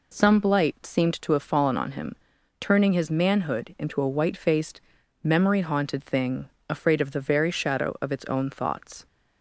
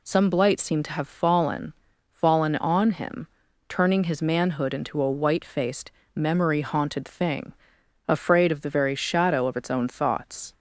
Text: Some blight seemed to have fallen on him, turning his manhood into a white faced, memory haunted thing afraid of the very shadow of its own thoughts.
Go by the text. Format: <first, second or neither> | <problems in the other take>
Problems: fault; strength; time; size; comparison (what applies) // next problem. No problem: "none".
first | says "fallen" twice; at 2.1 s // pauses between "thing" and "afraid"; noticeable; at 7.5 s; 0.54 s long; slight in the first